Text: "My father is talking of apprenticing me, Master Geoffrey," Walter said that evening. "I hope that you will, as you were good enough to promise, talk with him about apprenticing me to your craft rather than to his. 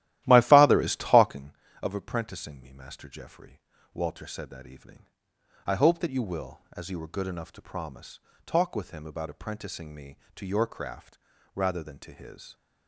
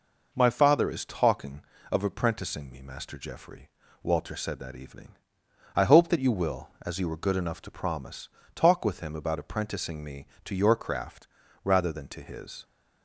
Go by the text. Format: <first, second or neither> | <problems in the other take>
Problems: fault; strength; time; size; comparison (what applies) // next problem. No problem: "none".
second | starts louder than the rest; strong; until 1.5 s; 14 dB // pauses between "craft" and "rather"; slight; at 11.1 s; 0.36 s long; slight in the second